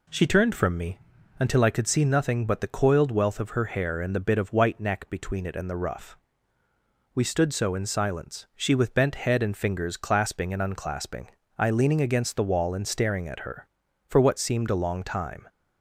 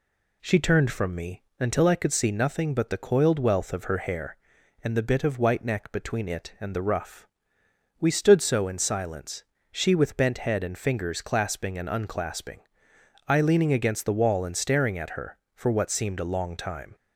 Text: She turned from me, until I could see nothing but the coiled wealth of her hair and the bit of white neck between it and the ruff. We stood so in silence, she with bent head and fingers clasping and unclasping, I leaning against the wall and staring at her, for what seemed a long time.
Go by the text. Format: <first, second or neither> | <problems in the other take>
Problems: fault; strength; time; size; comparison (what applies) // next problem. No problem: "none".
neither | none